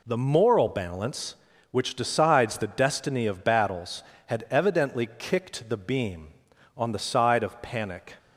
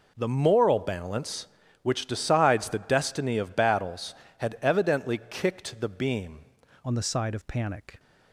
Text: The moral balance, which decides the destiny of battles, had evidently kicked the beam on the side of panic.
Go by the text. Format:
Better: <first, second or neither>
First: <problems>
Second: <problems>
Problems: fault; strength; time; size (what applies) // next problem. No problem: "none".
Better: first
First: none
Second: changes voice at "on"; from 6.8 s on; 1.1 s long